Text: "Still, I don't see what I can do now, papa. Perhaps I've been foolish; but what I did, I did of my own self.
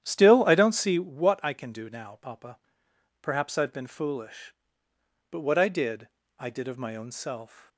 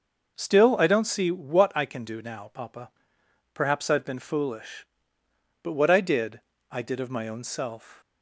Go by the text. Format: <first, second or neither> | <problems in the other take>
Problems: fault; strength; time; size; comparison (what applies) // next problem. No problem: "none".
second | starts louder than the rest; strong; until 1.2 s; 10.5 dB